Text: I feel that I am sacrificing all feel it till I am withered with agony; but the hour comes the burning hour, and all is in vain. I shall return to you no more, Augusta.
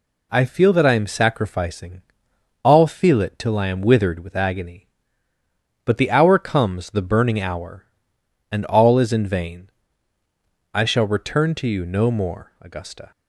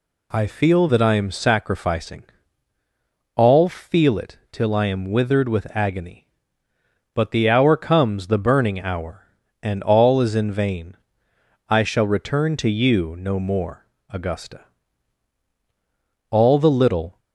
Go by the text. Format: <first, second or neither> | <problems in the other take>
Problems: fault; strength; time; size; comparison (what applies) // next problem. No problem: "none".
first | pauses between "sacrificing" and "all"; at 2.2 s; 1.1 s long; noticeable in the first // goes on to say "All the little"; noticeable; from 16.2 s on; 0.90 s long